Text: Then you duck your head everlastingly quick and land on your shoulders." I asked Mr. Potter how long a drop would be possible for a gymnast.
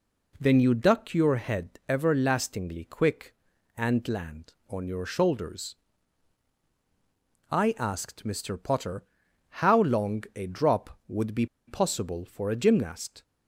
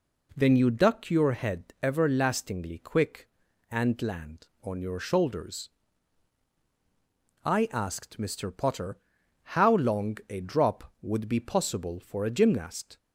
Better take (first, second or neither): second